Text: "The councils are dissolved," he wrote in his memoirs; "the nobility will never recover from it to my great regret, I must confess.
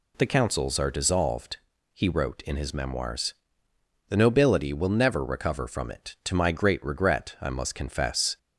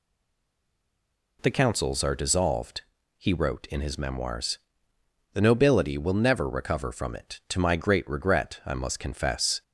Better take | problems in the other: first | stays silent before the first word; noticeable; until 1.3 s; 1.3 s long

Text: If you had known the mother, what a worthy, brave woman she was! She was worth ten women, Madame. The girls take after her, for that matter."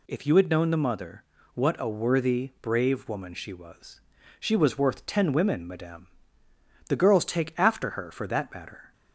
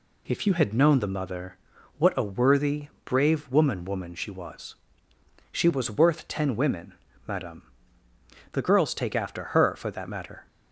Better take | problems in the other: first | says "woman" twice; at 3.8 s

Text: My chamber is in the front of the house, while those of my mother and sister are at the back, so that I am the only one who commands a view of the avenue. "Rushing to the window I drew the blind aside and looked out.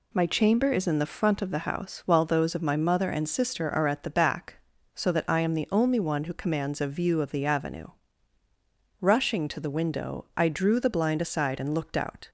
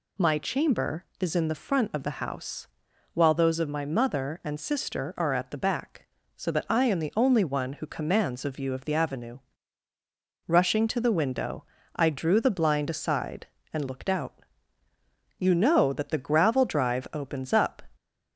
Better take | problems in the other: first | pauses between "window" and "I"; slight; at 11.6 s; 0.30 s long // goes on to say "You know that the gravel drive opens up"; strong; from 15.3 s on; 2.4 s long

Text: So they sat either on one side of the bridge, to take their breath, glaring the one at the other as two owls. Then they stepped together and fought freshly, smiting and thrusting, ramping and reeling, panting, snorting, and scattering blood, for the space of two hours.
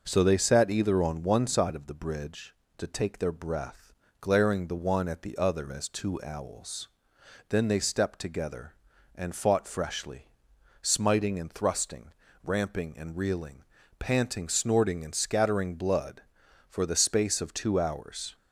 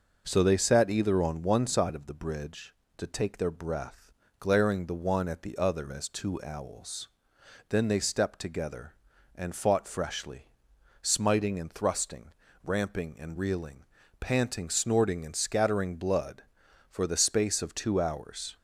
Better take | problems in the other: neither | none

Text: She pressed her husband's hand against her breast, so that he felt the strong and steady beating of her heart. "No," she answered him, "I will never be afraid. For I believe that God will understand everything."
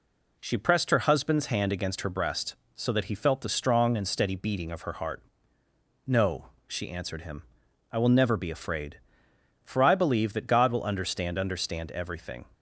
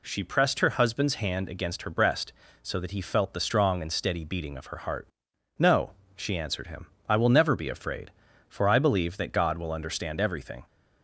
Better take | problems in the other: second | says "understand" twice; at 11.3 s

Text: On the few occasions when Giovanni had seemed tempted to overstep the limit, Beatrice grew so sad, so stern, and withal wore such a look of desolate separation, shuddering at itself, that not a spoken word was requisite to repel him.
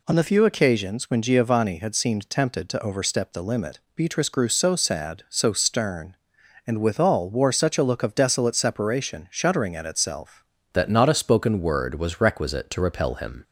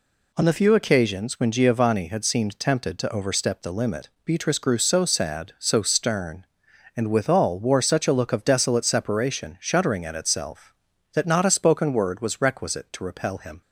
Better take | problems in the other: second | changes voice at "that"; from 10.7 s on; 2.7 s long

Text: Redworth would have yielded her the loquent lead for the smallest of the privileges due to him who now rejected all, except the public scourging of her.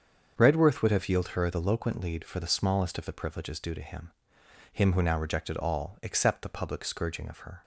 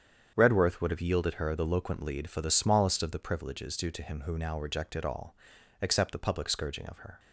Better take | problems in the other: second | starts louder than the rest; until 1.3 s; 7 dB; strong in the second // says "him" twice; at 4.7 s

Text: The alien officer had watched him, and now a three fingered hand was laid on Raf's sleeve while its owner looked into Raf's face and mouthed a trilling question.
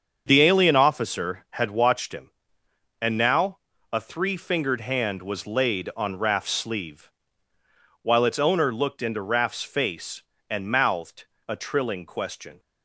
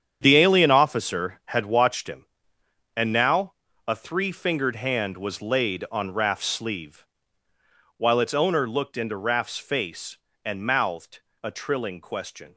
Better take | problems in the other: first | gets quieter; strong; throughout; 10.5 dB // starts louder than the rest; strong; until 1.2 s; 8.5 dB; also in the first // pauses between "now" and "a"; slight; at 3.5 s; 0.34 s long; slight in the first // pauses between "sleeve" and "while"; noticeable; at 7.0 s; 0.92 s long; noticeable in the first // pauses between "mouthed" and "a"; slight; at 11.1 s; 0.24 s long; slight in the first

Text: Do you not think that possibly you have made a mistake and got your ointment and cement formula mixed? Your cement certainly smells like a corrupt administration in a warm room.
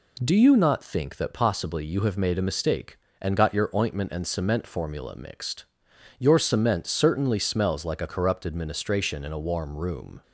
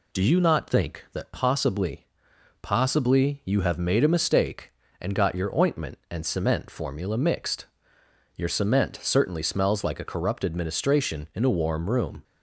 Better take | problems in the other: first | says "possibly" twice; at 2.6 s

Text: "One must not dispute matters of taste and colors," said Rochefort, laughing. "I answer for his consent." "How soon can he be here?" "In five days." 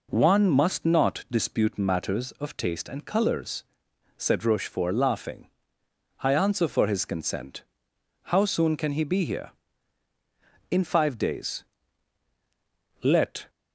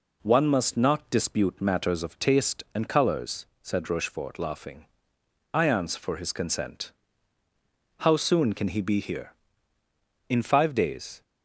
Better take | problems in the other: second | goes on to say "Let"; slight; from 13.0 s on; 0.46 s long

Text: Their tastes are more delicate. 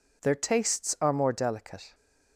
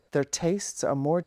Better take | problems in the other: first | stops before "delicate"; at 1.2 s

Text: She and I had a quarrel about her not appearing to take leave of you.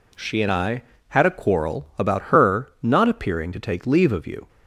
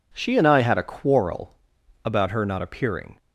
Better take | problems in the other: first | pauses between "quarrel" and "about"; noticeable; at 1.5 s; 0.48 s long // stops before "to take leave of you"; at 3.1 s

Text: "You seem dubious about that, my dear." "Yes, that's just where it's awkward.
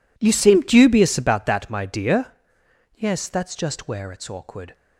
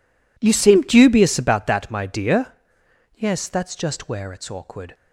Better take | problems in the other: neither | none

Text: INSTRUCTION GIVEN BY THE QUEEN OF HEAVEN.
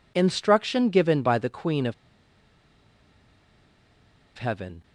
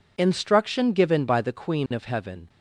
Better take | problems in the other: second | pauses between "OF" and "HEAVEN"; strong; at 1.9 s; 2.4 s long

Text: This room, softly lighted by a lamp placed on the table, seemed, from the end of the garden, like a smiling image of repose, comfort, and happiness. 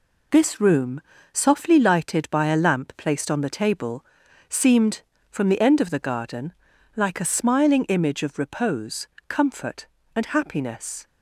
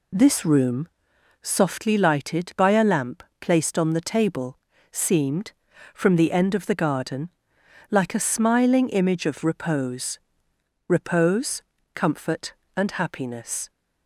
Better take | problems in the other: first | pauses between "lamp" and "placed"; slight; at 3.2 s; 0.16 s long // says "repose" twice; at 10.8 s

